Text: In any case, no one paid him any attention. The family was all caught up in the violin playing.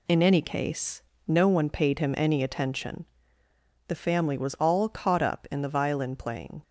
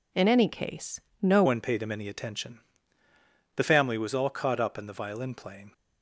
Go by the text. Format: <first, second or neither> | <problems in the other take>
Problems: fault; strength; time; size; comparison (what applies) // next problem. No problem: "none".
first | changes voice at "one"; from 1.4 s on; 4.3 s long